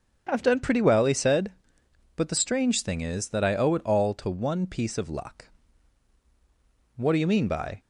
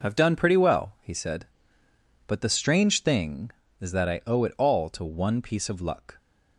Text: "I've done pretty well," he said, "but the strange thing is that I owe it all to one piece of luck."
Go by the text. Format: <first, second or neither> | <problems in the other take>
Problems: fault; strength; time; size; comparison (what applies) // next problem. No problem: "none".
second | starts louder than the rest; until 1.3 s; 7 dB // goes on to say "What do you mean by"; noticeable; from 6.9 s on; 0.82 s long